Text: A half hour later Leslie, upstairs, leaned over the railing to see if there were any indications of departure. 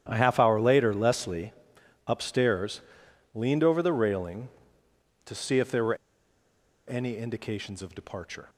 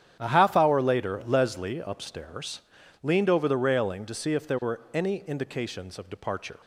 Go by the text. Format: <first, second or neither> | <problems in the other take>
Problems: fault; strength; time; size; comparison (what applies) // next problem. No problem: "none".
second | starts louder than the rest; strong; until 1.0 s; 11 dB; strong in the second // pauses between "were" and "any"; noticeable; at 5.9 s; 0.92 s long